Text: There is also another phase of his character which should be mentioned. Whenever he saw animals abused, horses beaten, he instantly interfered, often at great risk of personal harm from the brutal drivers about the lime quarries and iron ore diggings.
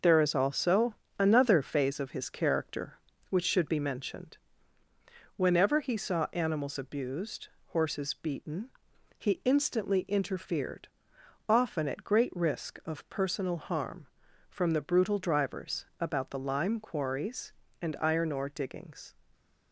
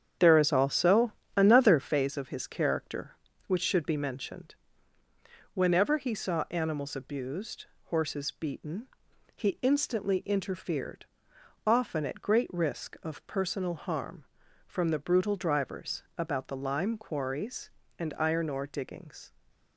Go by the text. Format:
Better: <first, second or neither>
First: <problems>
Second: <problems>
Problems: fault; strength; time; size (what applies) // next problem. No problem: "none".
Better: first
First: pauses between "also" and "another"; slight; at 0.9 s; 0.24 s long // pauses between "drivers" and "about"; slight; at 15.8 s; 0.16 s long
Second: starts louder than the rest; strong; until 1.9 s; 8.5 dB // pauses between "also" and "another"; slight; at 1.1 s; 0.24 s long // pauses between "drivers" and "about"; slight; at 16.0 s; 0.16 s long